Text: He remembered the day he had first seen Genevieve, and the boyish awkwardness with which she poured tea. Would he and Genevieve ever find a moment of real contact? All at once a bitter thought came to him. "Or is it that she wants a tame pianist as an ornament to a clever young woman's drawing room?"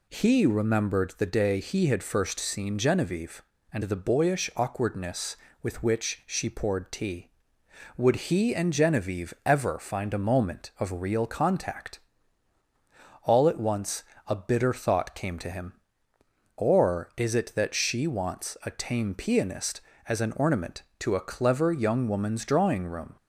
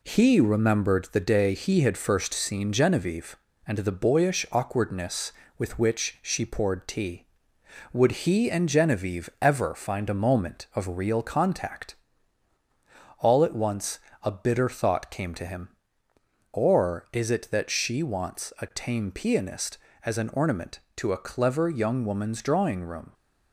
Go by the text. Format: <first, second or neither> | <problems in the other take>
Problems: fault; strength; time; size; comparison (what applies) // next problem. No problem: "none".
first | gets quieter; noticeable; throughout; 4 dB // pauses between "once" and "a"; slight; at 13.9 s; 0.24 s long; slight in the first